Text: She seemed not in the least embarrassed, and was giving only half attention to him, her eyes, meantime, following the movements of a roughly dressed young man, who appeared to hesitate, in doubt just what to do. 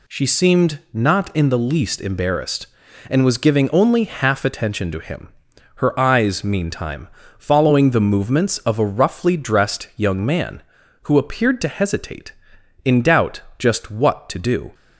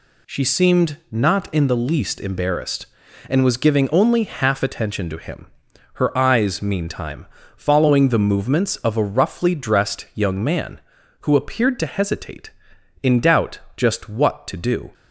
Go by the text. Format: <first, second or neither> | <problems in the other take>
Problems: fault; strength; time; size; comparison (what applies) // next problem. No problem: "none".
neither | pauses between "doubt" and "just"; slight; the same in both